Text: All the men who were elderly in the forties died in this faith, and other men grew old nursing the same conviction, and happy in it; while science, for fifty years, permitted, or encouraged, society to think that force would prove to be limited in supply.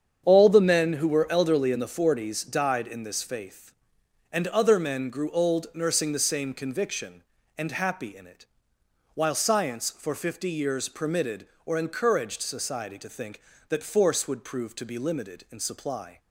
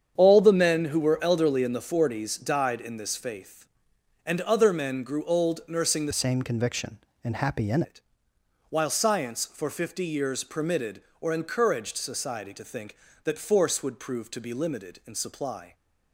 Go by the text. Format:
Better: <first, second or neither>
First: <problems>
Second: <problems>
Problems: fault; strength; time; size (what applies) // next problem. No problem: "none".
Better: first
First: starts louder than the rest; strong; until 1.2 s; 8 dB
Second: starts louder than the rest; strong; until 1.1 s; 8 dB // changes voice from "same" to "in"; from 6.1 to 7.8 s; 1.7 s long